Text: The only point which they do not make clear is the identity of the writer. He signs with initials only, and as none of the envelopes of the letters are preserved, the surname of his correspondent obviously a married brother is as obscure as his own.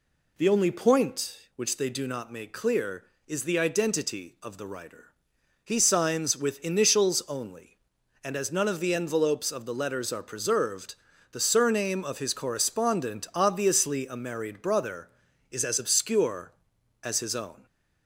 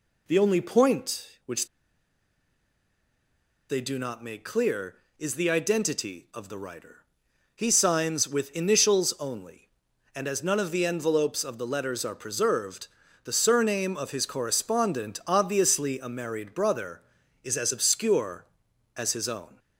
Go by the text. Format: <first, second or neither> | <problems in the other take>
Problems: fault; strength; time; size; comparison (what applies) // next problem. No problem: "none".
first | pauses between "which" and "they"; strong; at 1.6 s; 2.0 s long